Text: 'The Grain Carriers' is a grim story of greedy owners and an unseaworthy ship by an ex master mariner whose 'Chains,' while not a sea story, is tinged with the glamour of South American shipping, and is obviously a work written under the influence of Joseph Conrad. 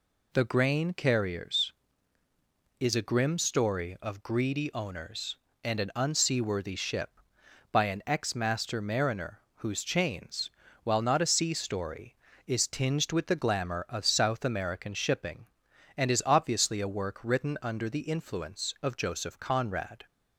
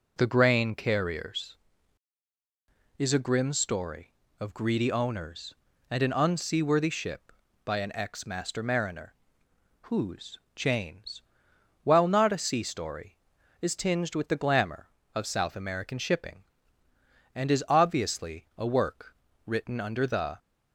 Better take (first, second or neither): first